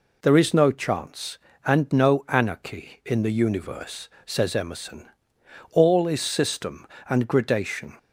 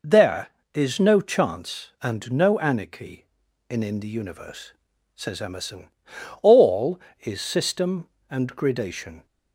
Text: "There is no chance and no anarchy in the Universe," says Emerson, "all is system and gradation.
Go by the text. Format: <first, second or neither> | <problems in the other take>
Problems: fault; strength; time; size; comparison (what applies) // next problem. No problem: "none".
first | says "in" twice; at 3.8 s